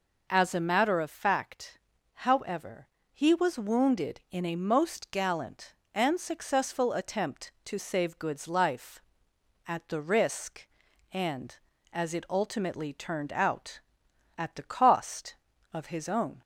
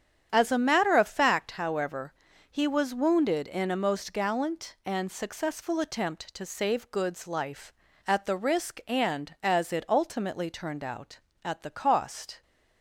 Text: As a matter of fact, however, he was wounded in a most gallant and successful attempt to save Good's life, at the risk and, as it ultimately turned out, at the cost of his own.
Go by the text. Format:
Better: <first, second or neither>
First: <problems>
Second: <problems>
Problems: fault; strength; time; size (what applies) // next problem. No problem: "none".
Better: first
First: none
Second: starts louder than the rest; strong; until 1.3 s; 8.5 dB // stops before "of his own"; at 12.4 s